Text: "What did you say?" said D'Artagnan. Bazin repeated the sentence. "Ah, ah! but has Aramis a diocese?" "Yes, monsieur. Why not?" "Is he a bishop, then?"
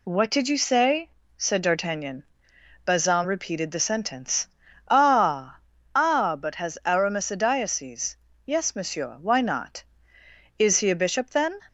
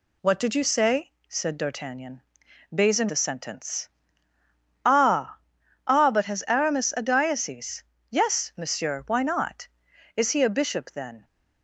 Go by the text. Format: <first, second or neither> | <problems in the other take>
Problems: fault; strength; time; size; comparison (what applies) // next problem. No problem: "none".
first | skips "repeated"; at 3.0 s